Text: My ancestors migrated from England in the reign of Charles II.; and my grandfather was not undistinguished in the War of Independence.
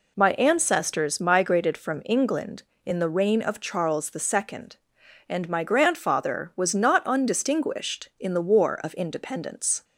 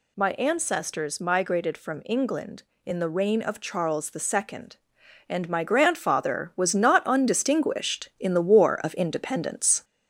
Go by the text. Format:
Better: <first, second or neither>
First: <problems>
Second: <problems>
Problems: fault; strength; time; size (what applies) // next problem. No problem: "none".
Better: first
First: none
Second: gets louder; slight; throughout; 3 dB